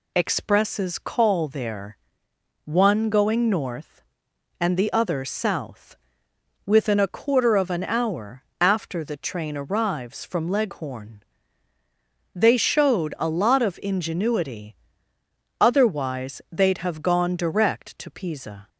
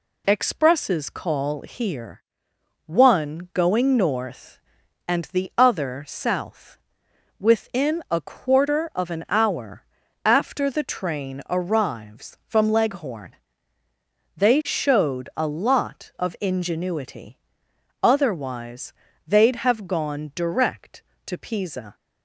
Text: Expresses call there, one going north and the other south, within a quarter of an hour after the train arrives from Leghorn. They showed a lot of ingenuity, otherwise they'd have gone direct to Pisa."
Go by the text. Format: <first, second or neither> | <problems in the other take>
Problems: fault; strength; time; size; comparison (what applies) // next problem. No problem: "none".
first | says "here" for "there"; at 1.5 s // pauses between "hour" and "after"; at 9.8 s; 0.40 s long; slight in the first // pauses between "otherwise" and "they'd"; slight; at 18.9 s; 0.34 s long